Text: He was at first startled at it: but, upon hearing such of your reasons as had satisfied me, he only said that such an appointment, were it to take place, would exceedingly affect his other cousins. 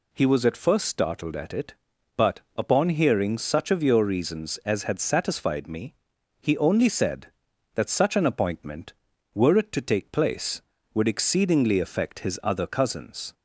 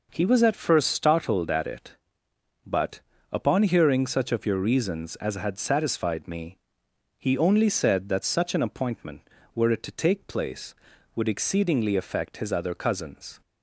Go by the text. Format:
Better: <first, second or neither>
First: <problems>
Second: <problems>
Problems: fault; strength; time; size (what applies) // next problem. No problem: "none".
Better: neither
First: none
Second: none